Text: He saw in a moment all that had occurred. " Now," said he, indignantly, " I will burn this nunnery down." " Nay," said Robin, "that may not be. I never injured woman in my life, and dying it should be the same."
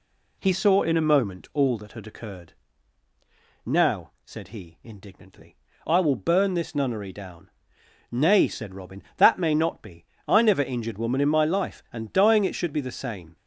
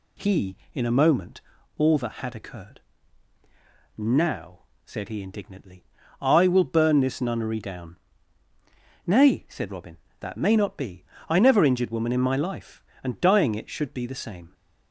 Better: first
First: none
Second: skips "saw"; at 0.6 s // pauses between "moment" and "all"; at 1.3 s; 0.38 s long

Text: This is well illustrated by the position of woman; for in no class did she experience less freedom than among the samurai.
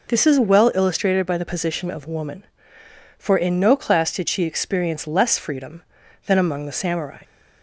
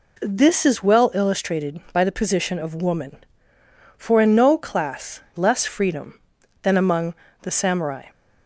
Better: first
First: none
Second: skips "did she experience"; at 5.2 s // pauses between "among" and "the"; slight; at 7.1 s; 0.26 s long

